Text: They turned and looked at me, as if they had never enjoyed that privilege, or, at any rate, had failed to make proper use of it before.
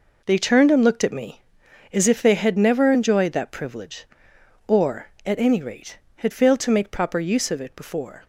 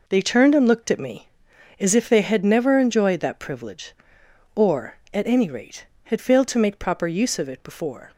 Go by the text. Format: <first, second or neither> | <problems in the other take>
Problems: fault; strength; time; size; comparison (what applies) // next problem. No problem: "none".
neither | none